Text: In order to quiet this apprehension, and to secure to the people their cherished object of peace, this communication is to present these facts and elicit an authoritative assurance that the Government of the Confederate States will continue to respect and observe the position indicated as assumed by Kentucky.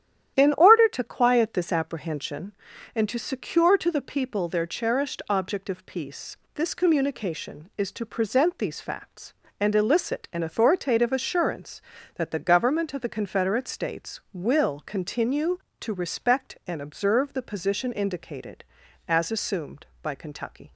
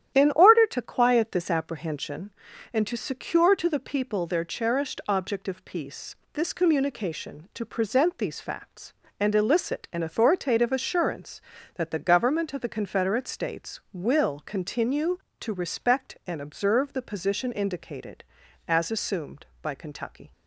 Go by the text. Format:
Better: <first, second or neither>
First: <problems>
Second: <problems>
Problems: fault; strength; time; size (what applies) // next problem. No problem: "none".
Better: first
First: starts louder than the rest; strong; until 1.4 s; 11 dB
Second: starts louder than the rest; strong; until 1.1 s; 11 dB // skips "is"; at 7.5 s